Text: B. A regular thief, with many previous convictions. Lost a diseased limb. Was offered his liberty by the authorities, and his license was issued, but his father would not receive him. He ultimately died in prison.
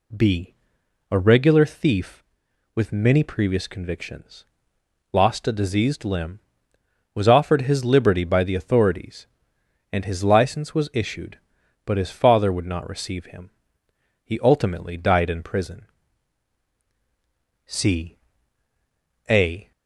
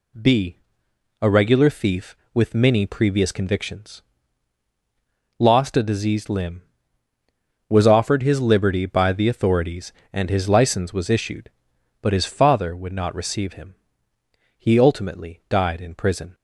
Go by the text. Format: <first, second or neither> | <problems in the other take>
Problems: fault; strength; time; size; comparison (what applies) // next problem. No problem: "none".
second | goes on to say "C A"; strong; from 17.6 s on; 2.0 s long